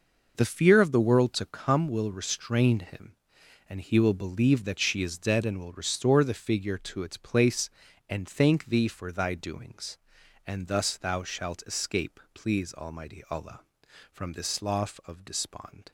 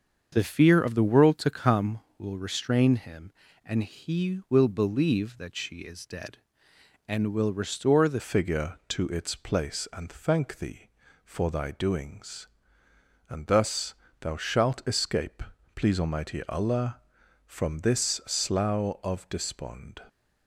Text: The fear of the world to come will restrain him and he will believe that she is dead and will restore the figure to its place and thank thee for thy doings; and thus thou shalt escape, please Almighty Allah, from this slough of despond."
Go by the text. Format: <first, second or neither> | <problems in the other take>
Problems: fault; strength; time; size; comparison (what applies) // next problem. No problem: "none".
first | starts louder than the rest; until 1.3 s; 7 dB // changes voice at "figure"; from 8.1 s on; 11.9 s long // pauses between "thus" and "thou"; slight; at 13.9 s; 0.28 s long